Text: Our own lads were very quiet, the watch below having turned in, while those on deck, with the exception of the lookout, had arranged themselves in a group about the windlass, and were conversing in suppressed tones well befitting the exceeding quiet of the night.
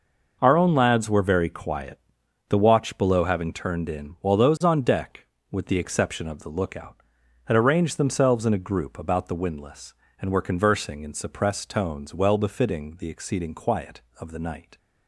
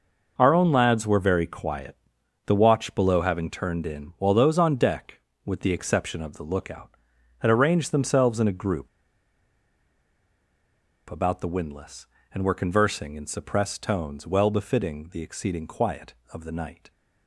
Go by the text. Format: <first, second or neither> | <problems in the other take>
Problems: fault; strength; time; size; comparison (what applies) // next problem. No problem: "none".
first | pauses between "group" and "about"; strong; at 8.8 s; 2.2 s long